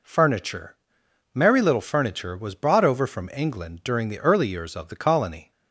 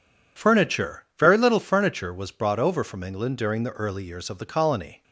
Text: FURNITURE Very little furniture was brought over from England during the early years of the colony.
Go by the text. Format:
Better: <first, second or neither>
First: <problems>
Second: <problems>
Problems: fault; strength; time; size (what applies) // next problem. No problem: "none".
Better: second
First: says "Merry" for "Very"; at 1.3 s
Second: none